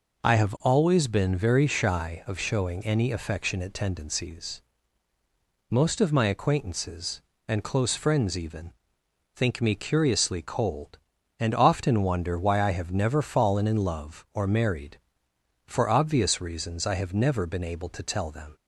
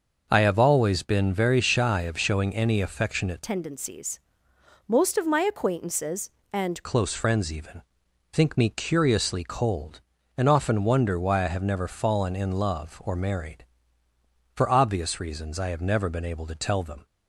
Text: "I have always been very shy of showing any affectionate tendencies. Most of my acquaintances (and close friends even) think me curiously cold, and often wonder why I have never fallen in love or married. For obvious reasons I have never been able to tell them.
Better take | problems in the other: first | changes voice from "tendencies" to "and"; from 3.4 to 6.8 s; 3.4 s long

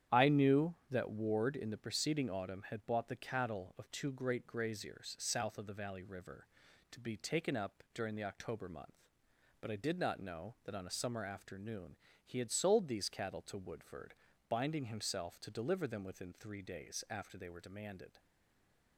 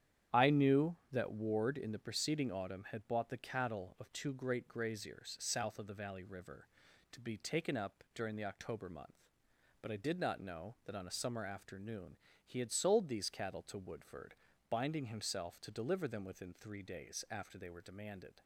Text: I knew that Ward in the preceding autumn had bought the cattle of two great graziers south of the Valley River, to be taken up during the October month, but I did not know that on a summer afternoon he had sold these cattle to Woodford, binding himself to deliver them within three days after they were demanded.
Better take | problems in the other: second | starts louder than the rest; strong; until 1.2 s; 9.5 dB; strong in the second // pauses between "afternoon" and "he"; slight; at 11.9 s; 0.30 s long; slight in the second // stays silent after the last word; slight; from 18.1 s on; 0.8 s long

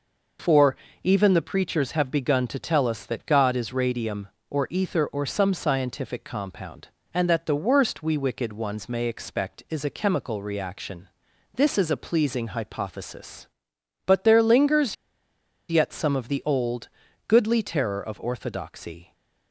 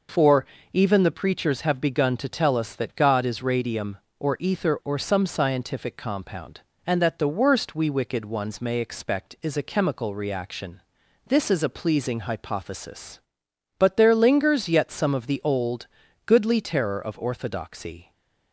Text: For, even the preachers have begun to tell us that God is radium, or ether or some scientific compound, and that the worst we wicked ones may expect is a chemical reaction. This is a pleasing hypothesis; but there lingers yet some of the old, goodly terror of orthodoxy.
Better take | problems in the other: second | pauses between "lingers" and "yet"; noticeable; at 14.9 s; 0.75 s long

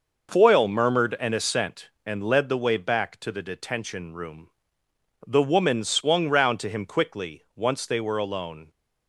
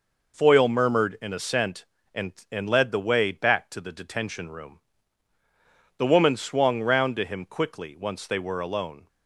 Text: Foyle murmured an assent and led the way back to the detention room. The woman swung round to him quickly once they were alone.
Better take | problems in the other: first | says "and" twice; at 2.5 s

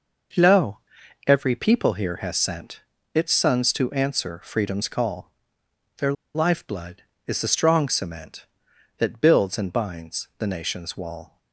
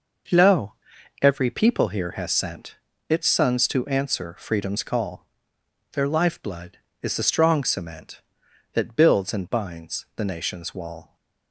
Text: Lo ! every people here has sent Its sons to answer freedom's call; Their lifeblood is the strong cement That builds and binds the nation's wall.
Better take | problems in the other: second | pauses between "sent" and "Its"; slight; at 2.8 s; 0.34 s long; slight in the second // pauses between "Their" and "lifeblood"; slight; at 6.1 s; 0.22 s long

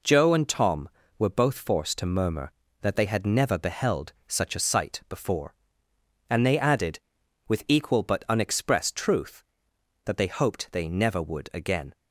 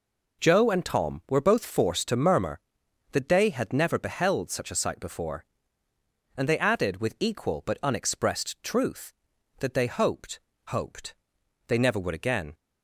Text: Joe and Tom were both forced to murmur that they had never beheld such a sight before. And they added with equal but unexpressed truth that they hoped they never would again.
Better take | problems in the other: first | says "hoped" twice; at 10.6 s

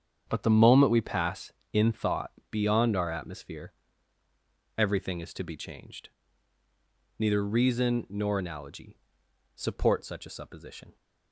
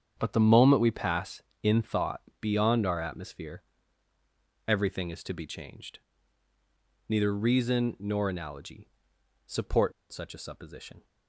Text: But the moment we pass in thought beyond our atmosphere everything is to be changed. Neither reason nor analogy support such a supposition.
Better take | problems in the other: first | starts louder than the rest; strong; until 1.1 s; 7.5 dB; strong in the first // pauses between "thought" and "beyond"; slight; at 2.2 s; 0.18 s long; slight in the first // pauses between "atmosphere" and "everything"; at 3.6 s; 1.0 s long; also in the first // pauses between "analogy" and "support"; noticeable; at 8.8 s; 0.56 s long; noticeable in the first // pauses between "support" and "such"; slight; at 9.9 s; 0.20 s long

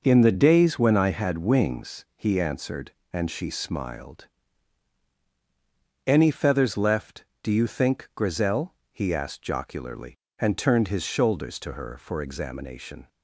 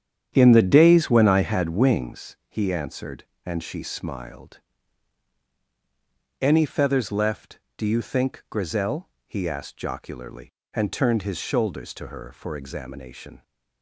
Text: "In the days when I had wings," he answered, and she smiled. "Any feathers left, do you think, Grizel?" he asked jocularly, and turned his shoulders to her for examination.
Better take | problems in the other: first | starts louder than the rest; strong; until 2.1 s; 9 dB

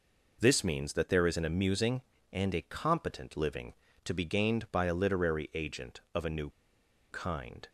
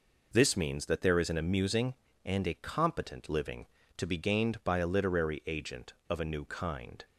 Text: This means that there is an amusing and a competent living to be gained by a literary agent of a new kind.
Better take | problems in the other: second | pauses between "new" and "kind"; noticeable; at 6.4 s; 0.60 s long

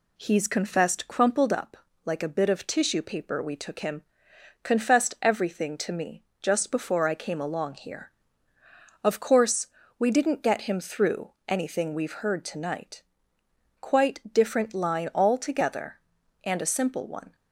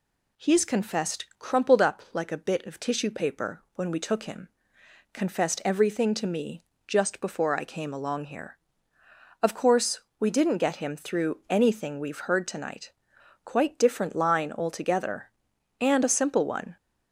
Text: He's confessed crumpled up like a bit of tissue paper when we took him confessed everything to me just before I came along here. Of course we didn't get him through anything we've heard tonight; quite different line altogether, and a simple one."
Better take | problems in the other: second | pauses between "up" and "like"; slight; at 1.7 s; 0.26 s long // skips "when"; at 3.4 s // pauses between "him" and "confessed"; noticeable; at 4.0 s; 0.62 s long; noticeable in the second // pauses between "me" and "just"; slight; at 6.2 s; 0.18 s long; slight in the second // pauses between "course" and "we"; slight; at 9.6 s; 0.32 s long; slight in the second // pauses between "through" and "anything"; slight; at 11.3 s; 0.16 s long

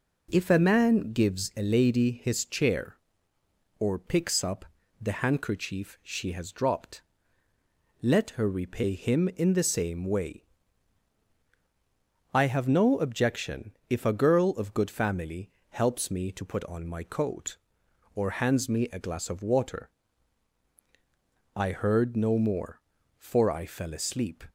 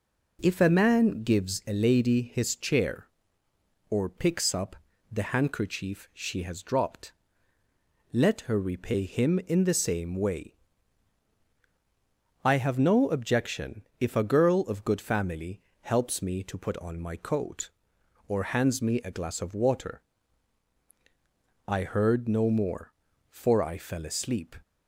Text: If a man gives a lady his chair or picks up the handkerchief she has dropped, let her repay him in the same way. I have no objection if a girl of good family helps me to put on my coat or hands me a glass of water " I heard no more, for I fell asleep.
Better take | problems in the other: neither | pauses between "up" and "the"; slight; the same in both // pauses between "objection" and "if"; slight; the same in both // pauses between "family" and "helps"; slight; the same in both

